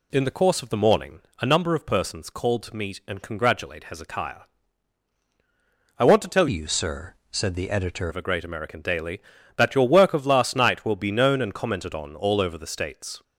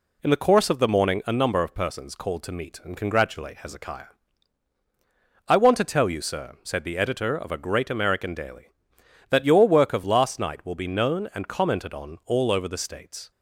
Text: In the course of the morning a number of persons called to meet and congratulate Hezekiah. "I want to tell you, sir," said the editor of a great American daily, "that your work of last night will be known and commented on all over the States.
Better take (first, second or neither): second